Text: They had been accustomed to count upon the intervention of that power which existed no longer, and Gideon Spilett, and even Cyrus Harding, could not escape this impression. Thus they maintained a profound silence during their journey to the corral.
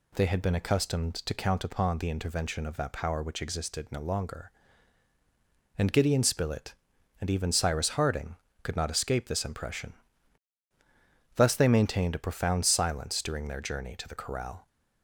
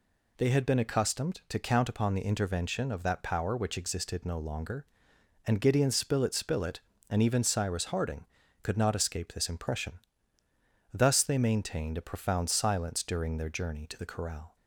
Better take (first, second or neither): first